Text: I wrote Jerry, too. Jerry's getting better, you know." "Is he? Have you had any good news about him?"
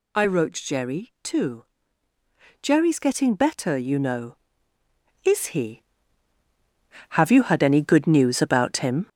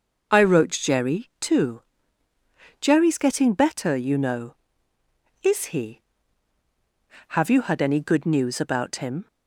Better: second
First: gets louder; noticeable; throughout; 5 dB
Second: none

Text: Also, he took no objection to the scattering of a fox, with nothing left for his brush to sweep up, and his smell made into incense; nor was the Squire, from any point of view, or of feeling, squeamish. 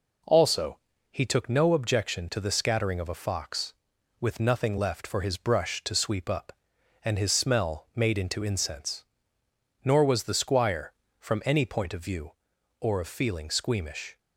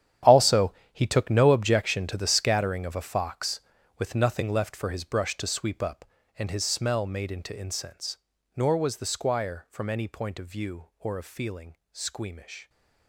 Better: first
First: none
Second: gets quieter; strong; throughout; 15 dB

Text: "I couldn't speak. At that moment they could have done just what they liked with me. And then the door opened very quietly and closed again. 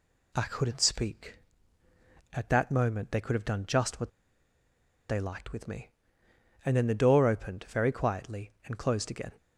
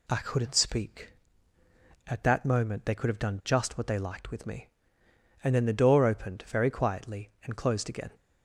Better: second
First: pauses between "what" and "they"; at 4.0 s; 0.99 s long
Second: none

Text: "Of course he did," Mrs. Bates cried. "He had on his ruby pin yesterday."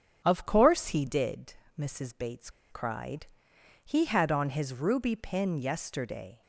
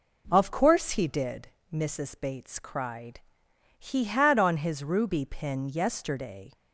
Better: second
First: starts louder than the rest; strong; until 1.2 s; 9 dB // pauses between "Bates" and "cried"; slight; at 2.4 s; 0.22 s long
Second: none

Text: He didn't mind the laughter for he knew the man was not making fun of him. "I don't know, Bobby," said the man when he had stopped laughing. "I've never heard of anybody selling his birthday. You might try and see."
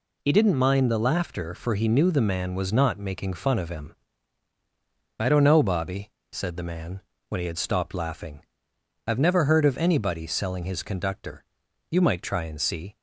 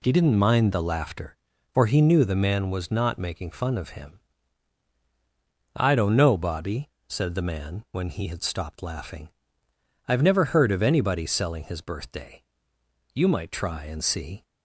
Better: second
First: pauses between "man" and "when"; slight; at 7.0 s; 0.28 s long // says "conductor" for "birthday"; at 10.8 s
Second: none

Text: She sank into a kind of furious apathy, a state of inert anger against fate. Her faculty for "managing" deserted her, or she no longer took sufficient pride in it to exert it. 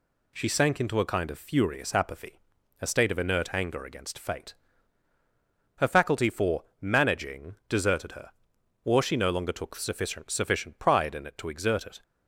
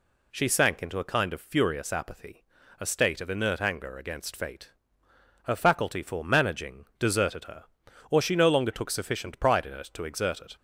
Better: second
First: pauses between "for" and "managing"; slight; at 6.6 s; 0.16 s long // says "sufficient" twice; at 10.3 s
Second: none

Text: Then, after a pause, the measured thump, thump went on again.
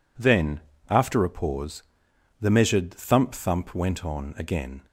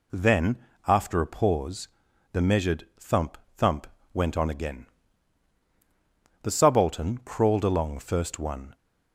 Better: first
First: none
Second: pauses between "thump" and "went"; slight; at 3.8 s; 0.26 s long // goes on to say "The Subaltern crawled along first one"; strong; from 6.4 s on; 2.3 s long

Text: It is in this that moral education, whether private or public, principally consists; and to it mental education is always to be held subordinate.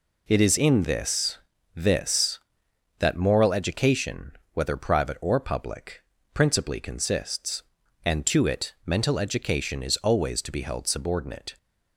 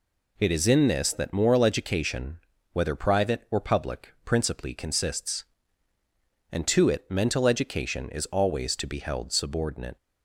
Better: second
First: says "this" twice; at 1.7 s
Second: none

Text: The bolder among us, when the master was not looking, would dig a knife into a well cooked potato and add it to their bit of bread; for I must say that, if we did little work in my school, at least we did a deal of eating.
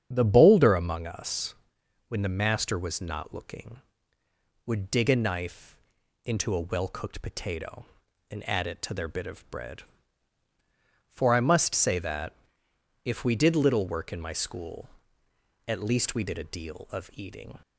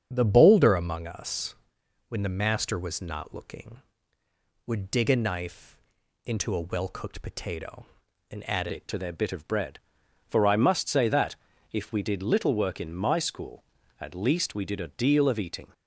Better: first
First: starts louder than the rest; strong; until 1.1 s; 8.5 dB // pauses between "knife" and "into"; noticeable; at 5.7 s; 0.48 s long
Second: starts louder than the rest; strong; until 1.1 s; 7.5 dB // pauses between "knife" and "into"; noticeable; at 5.7 s; 0.48 s long // changes voice at "it"; from 8.7 s on; 7.0 s long

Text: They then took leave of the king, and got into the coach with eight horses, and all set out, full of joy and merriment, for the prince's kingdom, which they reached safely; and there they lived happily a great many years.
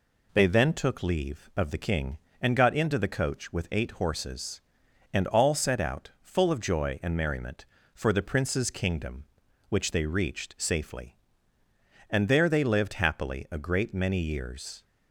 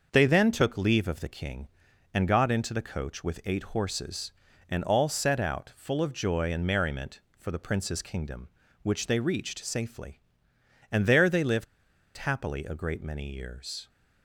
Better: first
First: none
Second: starts louder than the rest; until 1.1 s; 6 dB // pauses between "lived" and "happily"; noticeable; at 11.6 s; 0.53 s long

